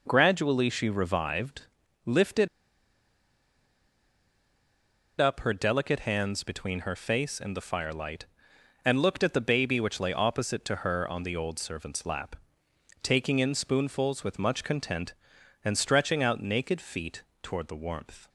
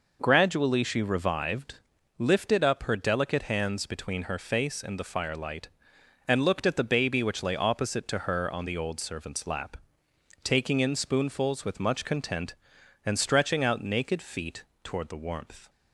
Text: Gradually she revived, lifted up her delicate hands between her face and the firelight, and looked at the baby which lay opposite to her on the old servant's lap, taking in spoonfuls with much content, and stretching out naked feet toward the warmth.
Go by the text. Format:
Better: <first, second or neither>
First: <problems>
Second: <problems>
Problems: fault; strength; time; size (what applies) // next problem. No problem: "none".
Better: second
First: pauses between "lifted" and "up"; strong; at 2.4 s; 2.7 s long // pauses between "feet" and "toward"; slight; at 17.2 s; 0.18 s long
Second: pauses between "feet" and "toward"; slight; at 14.6 s; 0.18 s long